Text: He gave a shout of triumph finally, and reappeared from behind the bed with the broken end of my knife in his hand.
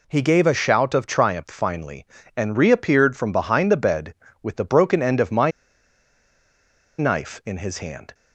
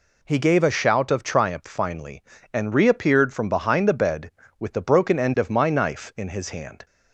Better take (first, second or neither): second